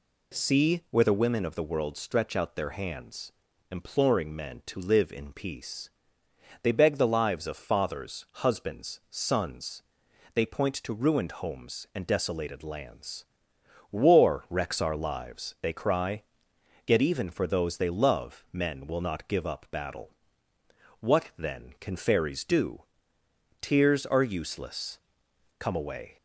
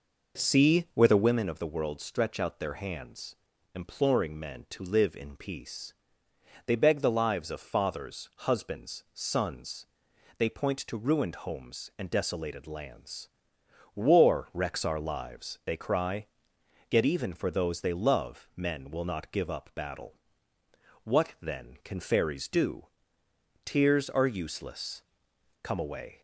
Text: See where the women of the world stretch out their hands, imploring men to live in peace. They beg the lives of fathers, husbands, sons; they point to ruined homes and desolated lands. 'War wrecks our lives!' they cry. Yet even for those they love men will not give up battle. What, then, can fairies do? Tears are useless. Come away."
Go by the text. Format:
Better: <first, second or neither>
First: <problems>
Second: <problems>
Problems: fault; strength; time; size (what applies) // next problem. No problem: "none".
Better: first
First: none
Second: starts louder than the rest; noticeable; until 1.5 s; 5 dB